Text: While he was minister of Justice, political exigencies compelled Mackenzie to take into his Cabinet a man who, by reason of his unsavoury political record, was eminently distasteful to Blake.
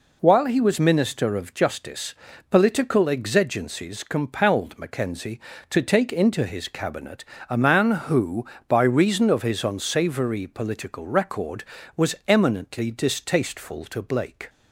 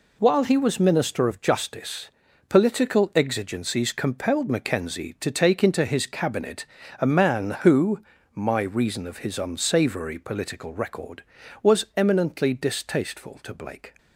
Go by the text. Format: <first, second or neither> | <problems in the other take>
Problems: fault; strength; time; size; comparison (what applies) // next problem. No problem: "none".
first | pauses between "Cabinet" and "a"; slight; at 6.6 s; 0.34 s long; slight in the first // says "my" for "by"; at 8.3 s